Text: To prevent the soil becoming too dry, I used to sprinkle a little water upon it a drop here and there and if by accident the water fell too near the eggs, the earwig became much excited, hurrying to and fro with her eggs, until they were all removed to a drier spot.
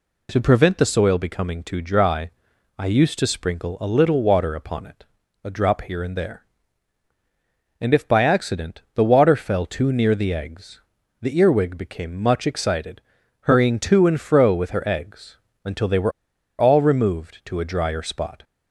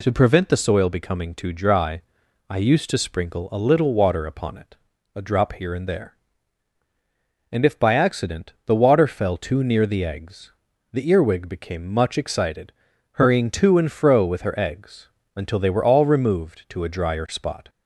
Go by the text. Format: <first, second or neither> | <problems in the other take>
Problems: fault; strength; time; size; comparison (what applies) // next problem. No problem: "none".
second | pauses between "it" and "a"; at 5.0 s; 0.38 s long; also in the second // pauses between "were" and "all"; noticeable; at 16.1 s; 0.47 s long